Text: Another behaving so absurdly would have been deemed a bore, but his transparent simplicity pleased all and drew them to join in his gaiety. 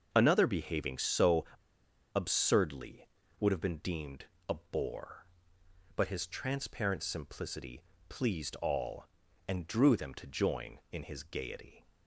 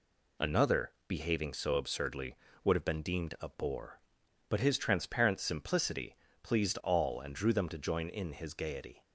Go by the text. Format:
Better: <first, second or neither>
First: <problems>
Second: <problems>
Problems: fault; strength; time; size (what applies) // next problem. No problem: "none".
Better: second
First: starts louder than the rest; until 1.1 s; 6 dB // pauses between "so" and "absurdly"; noticeable; at 1.4 s; 0.68 s long // pauses between "deemed" and "a"; slight; at 4.2 s; 0.22 s long // pauses between "simplicity" and "pleased"; slight; at 7.8 s; 0.26 s long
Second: pauses between "simplicity" and "pleased"; slight; at 6.1 s; 0.26 s long